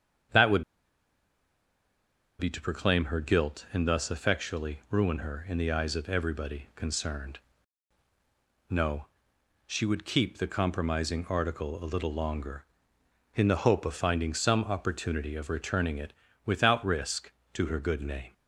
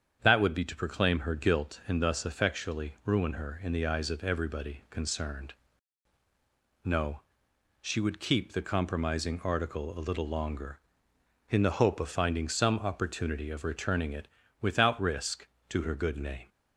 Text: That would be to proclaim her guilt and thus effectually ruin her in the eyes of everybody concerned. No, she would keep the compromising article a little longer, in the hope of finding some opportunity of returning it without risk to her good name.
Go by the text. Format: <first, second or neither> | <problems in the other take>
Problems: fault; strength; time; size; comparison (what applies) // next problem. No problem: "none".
second | starts louder than the rest; strong; until 3.0 s; 8 dB; strong in the second // pauses between "would" and "be"; strong; at 0.6 s; 1.7 s long // pauses between "it" and "without"; slight; at 16.1 s; 0.32 s long; slight in the second